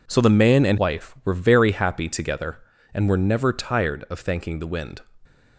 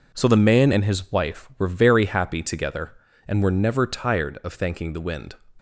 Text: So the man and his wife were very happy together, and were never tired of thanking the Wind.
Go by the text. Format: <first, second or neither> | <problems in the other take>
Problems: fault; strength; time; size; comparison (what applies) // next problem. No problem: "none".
second | skips "his"; at 0.7 s